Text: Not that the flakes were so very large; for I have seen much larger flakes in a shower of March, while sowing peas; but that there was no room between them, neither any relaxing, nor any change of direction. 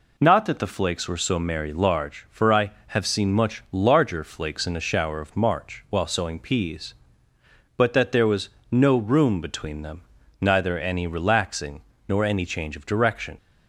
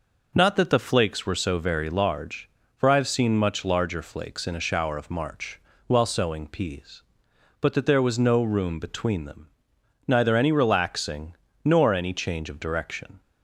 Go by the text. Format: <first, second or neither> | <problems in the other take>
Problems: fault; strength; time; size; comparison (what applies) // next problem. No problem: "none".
second | says "merry" for "very"; at 1.3 s // pauses between "was" and "no"; slight; at 8.4 s; 0.22 s long